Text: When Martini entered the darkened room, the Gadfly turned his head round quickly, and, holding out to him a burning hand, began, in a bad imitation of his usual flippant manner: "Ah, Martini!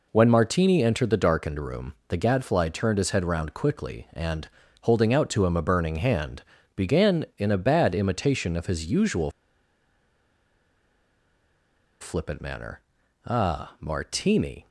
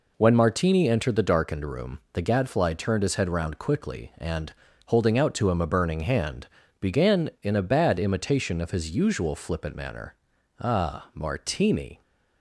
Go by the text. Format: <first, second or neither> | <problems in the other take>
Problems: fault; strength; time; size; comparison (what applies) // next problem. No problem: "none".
second | pauses between "usual" and "flippant"; strong; at 9.3 s; 2.7 s long